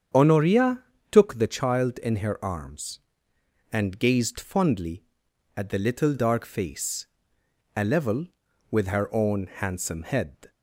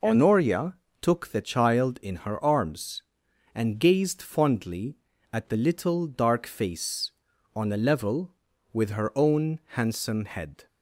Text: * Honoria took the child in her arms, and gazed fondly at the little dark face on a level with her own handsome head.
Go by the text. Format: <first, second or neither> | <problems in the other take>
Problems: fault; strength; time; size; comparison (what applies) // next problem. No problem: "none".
second | starts louder than the rest; strong; until 1.4 s; 8 dB // pauses between "Honoria" and "took"; slight; at 0.8 s; 0.28 s long; slight in the second // skips "on"; at 7.4 s